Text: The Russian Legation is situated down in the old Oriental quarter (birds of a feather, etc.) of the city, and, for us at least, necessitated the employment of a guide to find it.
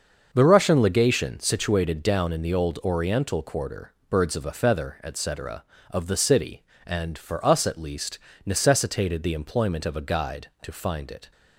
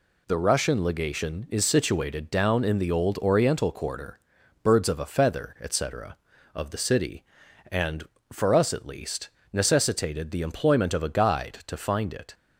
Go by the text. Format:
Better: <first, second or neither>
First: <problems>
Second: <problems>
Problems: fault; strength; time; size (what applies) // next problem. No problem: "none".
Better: second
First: starts louder than the rest; until 1.3 s; 6.5 dB // skips "is"; at 1.3 s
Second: none